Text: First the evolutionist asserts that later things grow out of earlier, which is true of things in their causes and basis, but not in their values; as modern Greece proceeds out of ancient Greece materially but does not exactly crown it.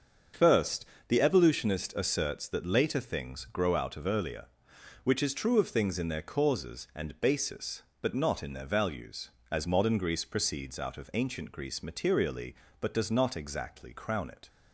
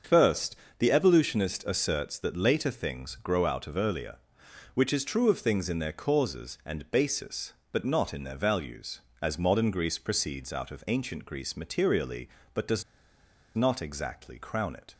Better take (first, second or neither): first